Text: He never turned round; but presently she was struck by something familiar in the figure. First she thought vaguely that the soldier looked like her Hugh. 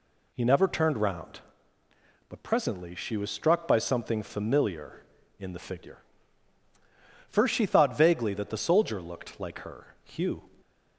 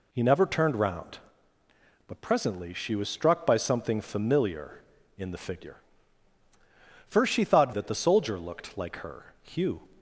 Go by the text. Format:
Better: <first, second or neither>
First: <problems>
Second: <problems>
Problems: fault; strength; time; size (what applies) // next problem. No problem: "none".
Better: first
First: none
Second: skips "vaguely"; at 7.7 s